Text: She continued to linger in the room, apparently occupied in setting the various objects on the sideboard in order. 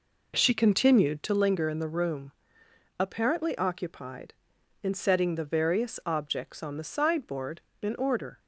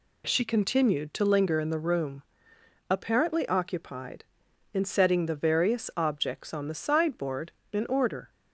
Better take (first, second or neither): second